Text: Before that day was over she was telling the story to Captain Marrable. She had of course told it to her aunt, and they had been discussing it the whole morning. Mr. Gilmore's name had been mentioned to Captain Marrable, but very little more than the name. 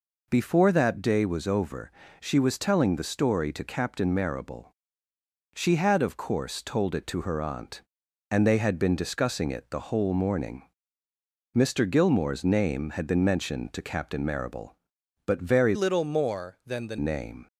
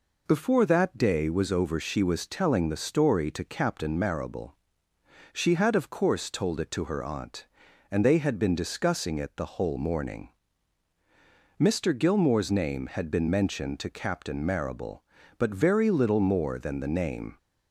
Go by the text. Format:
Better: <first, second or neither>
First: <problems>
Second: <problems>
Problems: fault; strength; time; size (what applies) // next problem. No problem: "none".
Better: second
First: pauses between "over" and "she"; slight; at 1.9 s; 0.30 s long // changes voice from "little" to "the"; from 15.7 to 16.9 s; 1.2 s long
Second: none